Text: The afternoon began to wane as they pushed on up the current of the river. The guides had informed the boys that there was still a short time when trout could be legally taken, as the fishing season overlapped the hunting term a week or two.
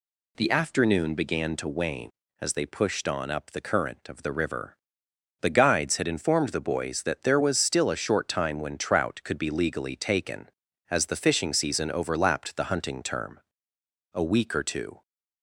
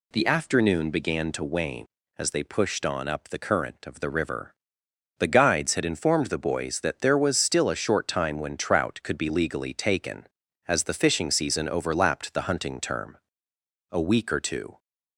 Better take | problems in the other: neither | pauses between "term" and "a"; noticeable; the same in both

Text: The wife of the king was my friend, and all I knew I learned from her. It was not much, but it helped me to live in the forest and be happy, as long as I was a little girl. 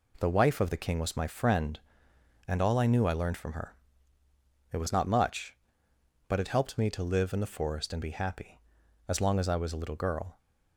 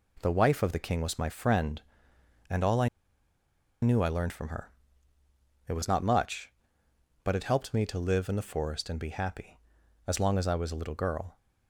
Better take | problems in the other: first | pauses between "I" and "knew"; noticeable; at 2.8 s; 0.94 s long

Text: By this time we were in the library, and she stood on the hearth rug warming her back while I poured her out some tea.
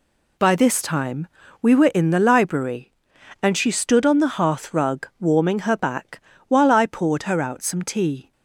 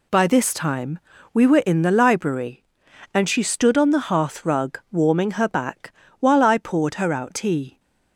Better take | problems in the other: first | pauses between "time" and "we"; slight; at 0.9 s; 0.36 s long; slight in the first // pauses between "back" and "while"; slight; at 5.9 s; 0.26 s long; slight in the first // skips "some"; at 7.3 s

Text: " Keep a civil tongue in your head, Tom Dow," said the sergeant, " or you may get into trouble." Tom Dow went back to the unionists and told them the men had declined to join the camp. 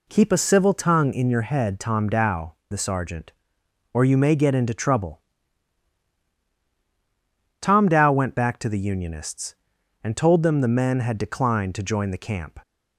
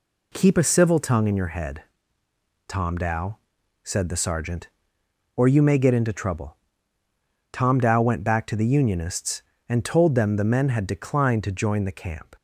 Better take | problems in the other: second | skips "said"; at 2.6 s

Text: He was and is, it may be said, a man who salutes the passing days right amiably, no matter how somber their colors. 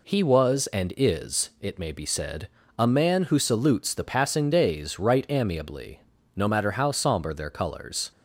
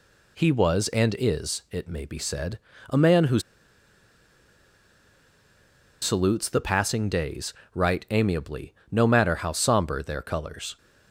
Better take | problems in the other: first | pauses between "who" and "salutes"; strong; at 3.3 s; 2.6 s long // pauses between "days" and "right"; slight; at 7.5 s; 0.22 s long

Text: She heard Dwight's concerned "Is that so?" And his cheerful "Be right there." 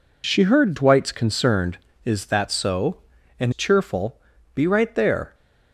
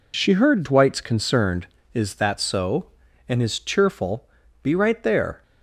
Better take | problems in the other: second | skips "his"; at 3.5 s // pauses between "cheerful" and "Be"; slight; at 4.1 s; 0.34 s long; slight in the second

